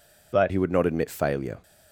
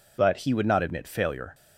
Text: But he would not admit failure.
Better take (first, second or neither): second